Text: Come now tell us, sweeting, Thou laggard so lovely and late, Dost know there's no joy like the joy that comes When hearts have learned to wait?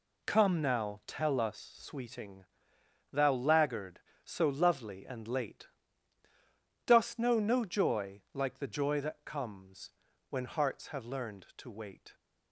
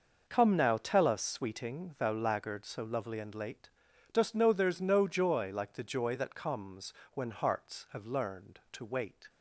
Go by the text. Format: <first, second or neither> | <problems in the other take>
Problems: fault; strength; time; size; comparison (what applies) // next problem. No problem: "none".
second | skips "there's"; at 7.3 s // pauses between "comes" and "When"; at 9.9 s; 0.38 s long; slight in the second